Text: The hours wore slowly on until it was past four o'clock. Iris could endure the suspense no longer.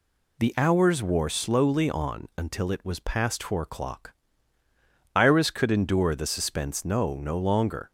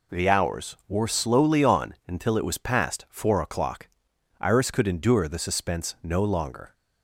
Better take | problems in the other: second | says "no" twice; at 7.1 s

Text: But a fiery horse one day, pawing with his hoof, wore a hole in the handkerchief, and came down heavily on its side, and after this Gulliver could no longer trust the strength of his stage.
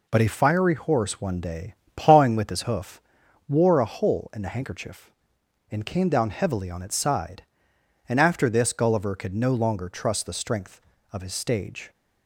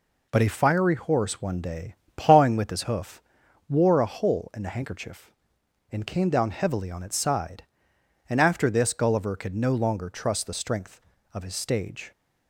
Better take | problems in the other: neither | none

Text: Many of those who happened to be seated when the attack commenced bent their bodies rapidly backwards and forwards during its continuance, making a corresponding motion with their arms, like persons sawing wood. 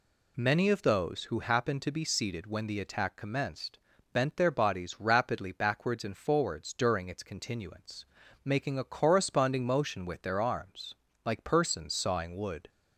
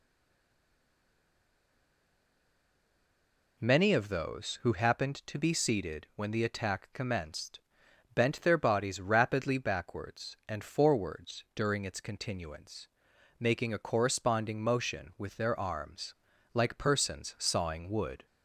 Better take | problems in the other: first | stays silent before the first word; strong; until 3.5 s; 3.5 s long // pauses between "commenced" and "bent"; noticeable; at 7.5 s; 0.54 s long; slight in the first

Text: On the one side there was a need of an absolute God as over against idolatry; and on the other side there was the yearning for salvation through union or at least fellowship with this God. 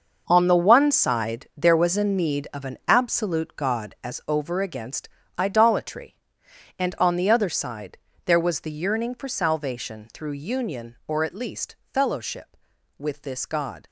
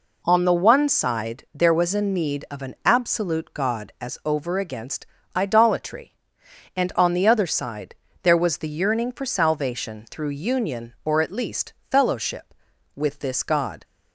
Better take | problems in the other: second | gets quieter; strong; throughout; 12 dB // pauses between "against" and "idolatry"; slight; at 5.0 s; 0.30 s long; slight in the second // pauses between "side" and "there"; slight; at 7.9 s; 0.28 s long; slight in the second // pauses between "least" and "fellowship"; slight; at 11.7 s; 0.16 s long; slight in the second

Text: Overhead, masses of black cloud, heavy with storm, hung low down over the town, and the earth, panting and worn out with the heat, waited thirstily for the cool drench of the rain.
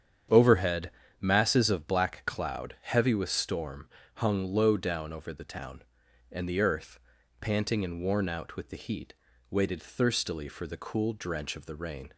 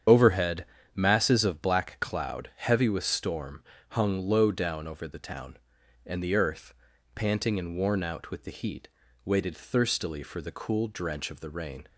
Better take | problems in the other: first | loses the start of "Overhead"; at 0.0 s; 45 ms // starts louder than the rest; strong; until 1.3 s; 8.5 dB; strong in the first

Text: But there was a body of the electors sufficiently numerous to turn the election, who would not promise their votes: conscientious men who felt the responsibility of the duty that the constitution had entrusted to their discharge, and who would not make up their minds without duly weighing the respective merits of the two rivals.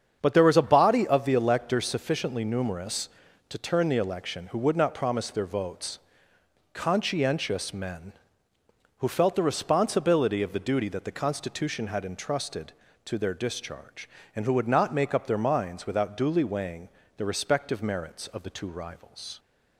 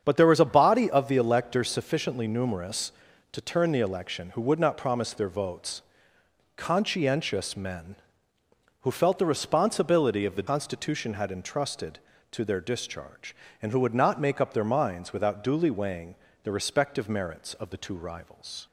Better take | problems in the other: first | starts louder than the rest; strong; until 1.0 s; 7.5 dB; strong in the first // skips "duty that the"; at 10.4 s // pauses between "weighing" and "the"; slight; at 16.1 s; 0.26 s long; slight in the first

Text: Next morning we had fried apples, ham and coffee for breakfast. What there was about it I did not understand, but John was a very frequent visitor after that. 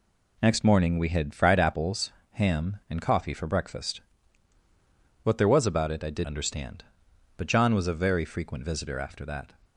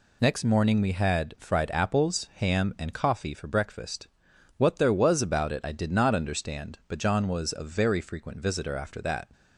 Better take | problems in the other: second | skips "not"; at 6.2 s

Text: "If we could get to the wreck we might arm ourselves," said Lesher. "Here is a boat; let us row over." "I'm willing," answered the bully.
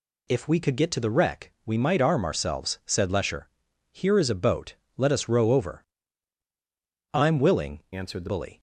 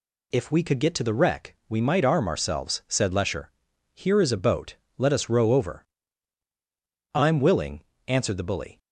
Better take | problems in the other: second | changes voice from "answered" to "the"; from 7.9 to 8.2 s; 0.3 s long

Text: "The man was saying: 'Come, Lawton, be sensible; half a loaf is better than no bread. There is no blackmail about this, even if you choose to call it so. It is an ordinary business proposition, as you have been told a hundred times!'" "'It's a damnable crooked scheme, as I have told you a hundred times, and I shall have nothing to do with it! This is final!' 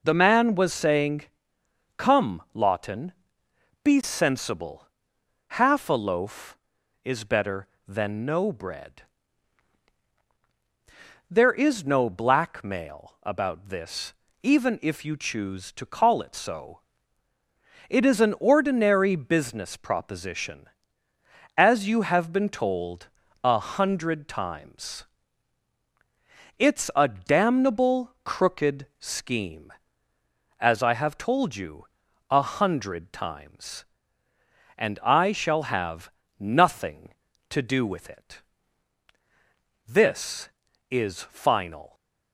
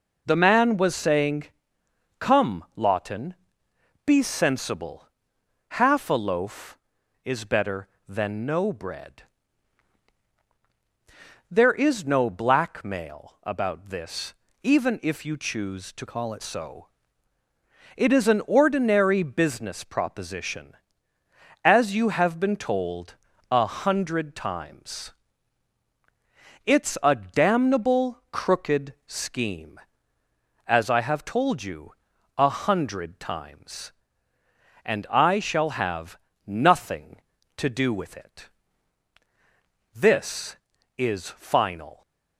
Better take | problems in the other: first | changes voice from "call" to "it"; from 16.0 to 16.4 s; 0.4 s long // pauses between "told" and "a"; slight; at 23.1 s; 0.34 s long; slight in the first // pauses between "you" and "a"; at 31.9 s; 0.44 s long; also in the first // pauses between "have" and "nothing"; slight; at 36.1 s; 0.28 s long; slight in the first

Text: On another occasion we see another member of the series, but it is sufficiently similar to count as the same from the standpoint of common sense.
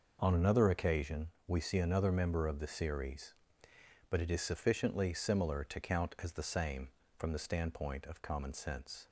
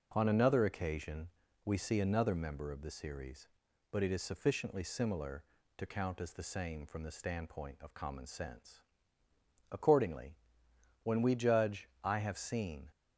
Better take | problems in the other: first | pauses between "occasion" and "we"; slight; at 1.2 s; 0.36 s long; slight in the first // goes on to say "Accordingly when we judge I have seen"; strong; from 9.7 s on; 3.2 s long

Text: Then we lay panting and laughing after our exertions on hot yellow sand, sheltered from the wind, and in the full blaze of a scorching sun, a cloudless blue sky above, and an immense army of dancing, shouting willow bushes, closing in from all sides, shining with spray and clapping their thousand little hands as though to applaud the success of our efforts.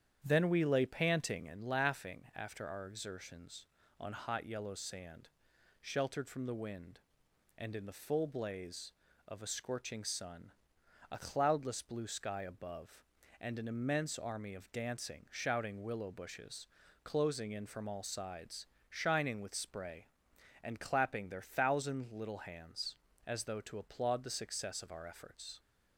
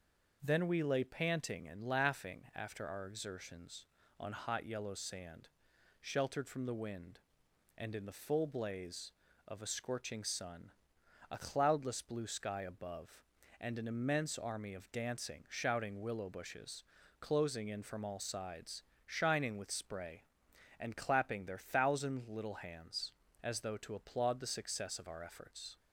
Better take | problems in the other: second | starts louder than the rest; strong; until 1.7 s; 9 dB

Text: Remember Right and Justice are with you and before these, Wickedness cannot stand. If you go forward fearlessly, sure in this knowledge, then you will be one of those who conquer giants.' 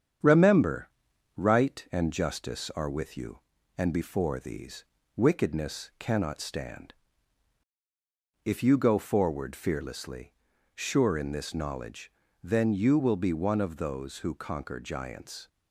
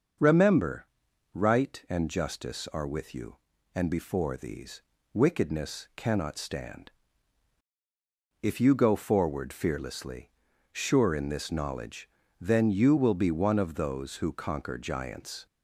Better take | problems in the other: second | gets quieter; throughout; 3.5 dB // starts louder than the rest; strong; until 1.7 s; 8 dB; also in the second // pauses between "Remember" and "Right"; noticeable; at 0.8 s; 0.48 s long; noticeable in the second

